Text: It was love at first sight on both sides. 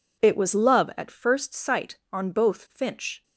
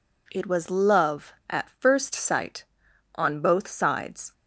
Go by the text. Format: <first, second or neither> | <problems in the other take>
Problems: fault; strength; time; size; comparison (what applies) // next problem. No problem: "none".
second | says "finch" for "sides"; at 2.6 s